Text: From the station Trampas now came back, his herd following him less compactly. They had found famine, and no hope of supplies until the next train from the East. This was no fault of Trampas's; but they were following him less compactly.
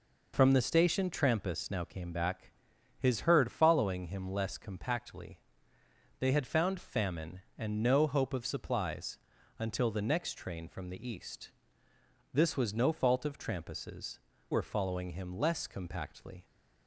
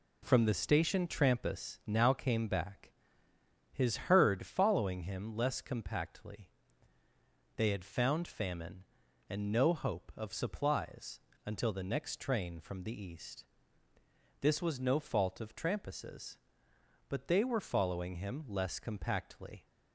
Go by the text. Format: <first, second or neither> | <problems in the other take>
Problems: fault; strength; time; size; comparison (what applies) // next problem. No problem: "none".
second | pauses between "supplies" and "until"; at 9.1 s; 0.44 s long; slight in the second // skips "but they"; at 14.3 s